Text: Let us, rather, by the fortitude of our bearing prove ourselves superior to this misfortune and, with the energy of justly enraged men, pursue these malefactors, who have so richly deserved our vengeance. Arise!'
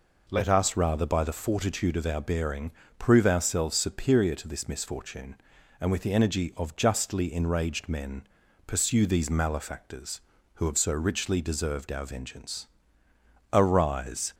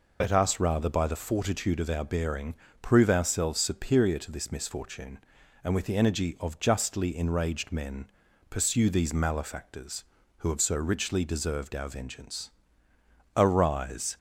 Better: first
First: pauses between "bearing" and "prove"; slight; at 2.6 s; 0.28 s long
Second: loses the start of "Let"; at 0.2 s; 75 ms // pauses between "bearing" and "prove"; slight; at 2.5 s; 0.28 s long

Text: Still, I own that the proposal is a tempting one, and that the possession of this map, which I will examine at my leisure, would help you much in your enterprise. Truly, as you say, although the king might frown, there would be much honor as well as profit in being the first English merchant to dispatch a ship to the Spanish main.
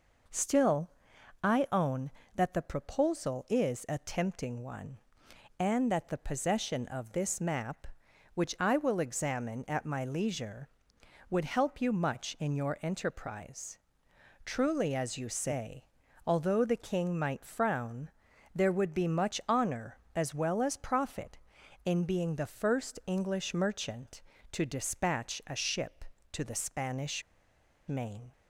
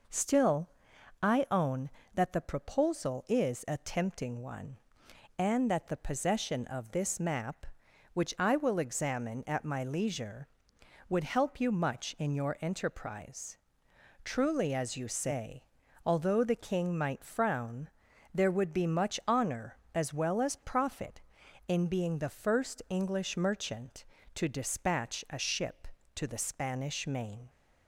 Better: second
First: pauses between "Spanish" and "main"; noticeable; at 27.2 s; 0.67 s long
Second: none

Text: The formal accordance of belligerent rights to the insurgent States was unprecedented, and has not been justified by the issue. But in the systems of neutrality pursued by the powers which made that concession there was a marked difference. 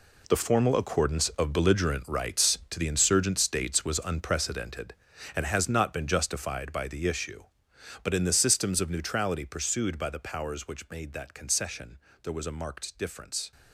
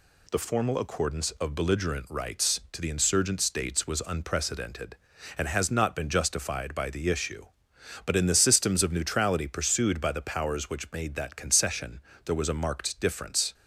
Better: second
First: gets quieter; strong; throughout; 12 dB // pauses between "concession" and "there"; slight; at 11.9 s; 0.24 s long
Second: pauses between "concession" and "there"; slight; at 12.0 s; 0.24 s long

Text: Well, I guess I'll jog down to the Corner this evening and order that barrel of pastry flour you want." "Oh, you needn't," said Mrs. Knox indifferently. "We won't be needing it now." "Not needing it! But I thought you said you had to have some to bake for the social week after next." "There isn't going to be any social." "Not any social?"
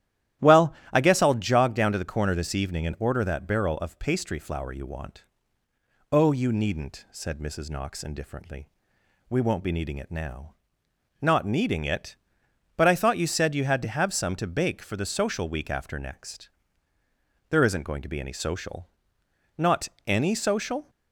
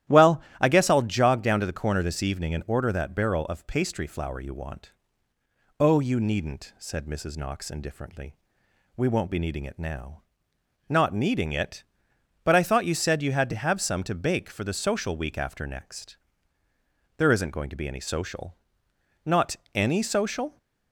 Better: neither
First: starts louder than the rest; strong; until 1.5 s; 12.5 dB // pauses between "Not" and "any"; slight; at 19.8 s; 0.18 s long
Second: starts louder than the rest; strong; until 1.2 s; 12.5 dB // pauses between "Not" and "any"; slight; at 19.5 s; 0.18 s long

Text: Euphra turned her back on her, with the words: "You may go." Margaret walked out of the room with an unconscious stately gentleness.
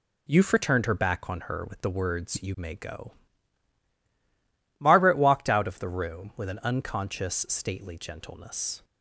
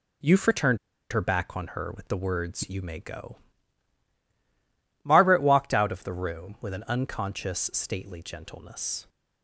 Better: first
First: none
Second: pauses between "turned" and "her"; slight; at 0.7 s; 0.34 s long

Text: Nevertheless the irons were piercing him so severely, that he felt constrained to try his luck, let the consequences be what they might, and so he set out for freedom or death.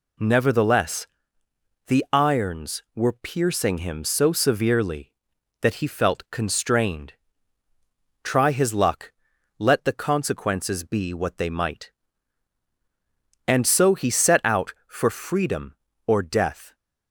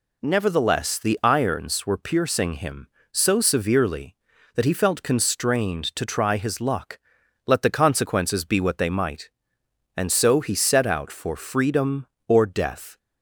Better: second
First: pauses between "Nevertheless" and "the"; noticeable; at 1.0 s; 0.80 s long // skips "to"; at 7.6 s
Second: none

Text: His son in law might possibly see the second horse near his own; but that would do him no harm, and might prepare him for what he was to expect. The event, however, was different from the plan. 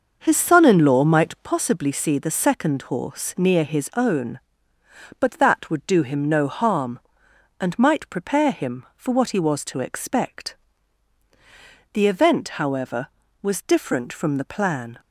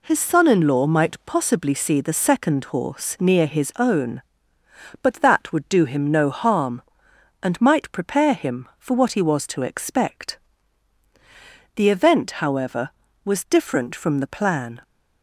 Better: second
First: starts louder than the rest; noticeable; until 1.4 s; 6 dB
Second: none

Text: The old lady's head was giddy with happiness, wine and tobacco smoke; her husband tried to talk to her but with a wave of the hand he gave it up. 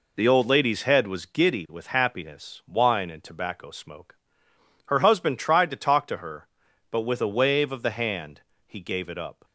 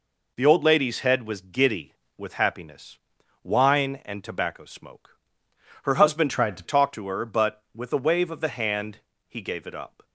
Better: first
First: pauses between "hand" and "he"; slight; at 8.4 s; 0.26 s long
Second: changes voice from "tried" to "to"; from 6.3 to 6.6 s; 0.3 s long // pauses between "hand" and "he"; slight; at 9.0 s; 0.26 s long

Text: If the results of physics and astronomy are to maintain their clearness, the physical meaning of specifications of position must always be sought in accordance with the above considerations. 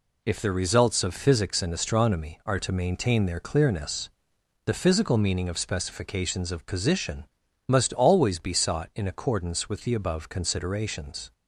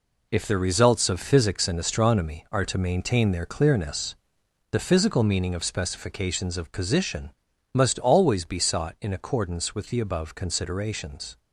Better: first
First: pauses between "position" and "must"; at 7.2 s; 0.42 s long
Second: gets quieter; strong; throughout; 8.5 dB // pauses between "position" and "must"; at 7.3 s; 0.42 s long

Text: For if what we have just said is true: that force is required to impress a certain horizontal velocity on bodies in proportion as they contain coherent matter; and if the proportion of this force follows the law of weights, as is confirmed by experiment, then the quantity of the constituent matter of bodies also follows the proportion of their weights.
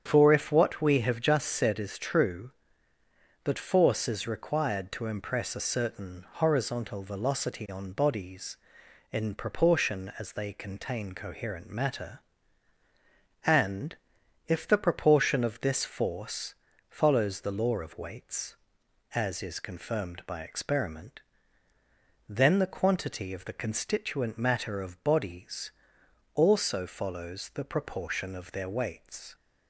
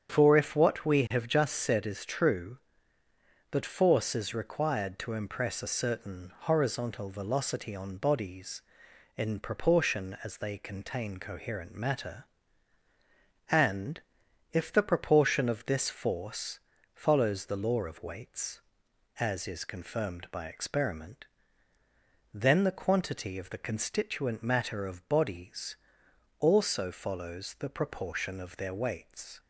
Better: neither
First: starts louder than the rest; strong; until 1.0 s; 8 dB // pauses between "and" and "if"; noticeable; at 13.9 s; 0.50 s long // pauses between "force" and "follows"; slight; at 16.5 s; 0.34 s long // pauses between "bodies" and "also"; noticeable; at 25.7 s; 0.62 s long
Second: starts louder than the rest; strong; until 1.1 s; 8 dB // pauses between "and" and "if"; noticeable; at 14.0 s; 0.50 s long // pauses between "force" and "follows"; slight; at 16.5 s; 0.34 s long // pauses between "bodies" and "also"; noticeable; at 25.7 s; 0.62 s long

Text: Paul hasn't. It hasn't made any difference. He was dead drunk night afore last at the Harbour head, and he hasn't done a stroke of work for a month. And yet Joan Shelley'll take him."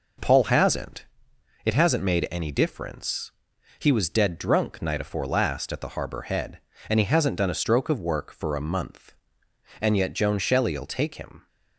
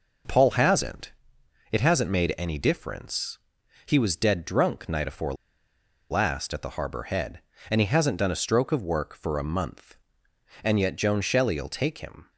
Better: first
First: none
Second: pauses between "afore" and "last"; noticeable; at 5.3 s; 0.76 s long

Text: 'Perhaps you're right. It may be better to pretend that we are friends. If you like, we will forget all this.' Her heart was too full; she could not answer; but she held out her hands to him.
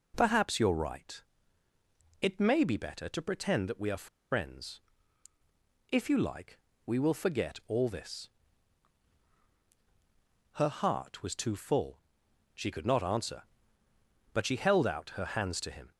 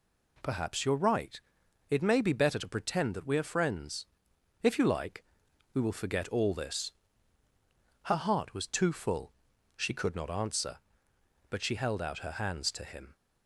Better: second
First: pauses between "are" and "friends"; slight; at 4.0 s; 0.23 s long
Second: none

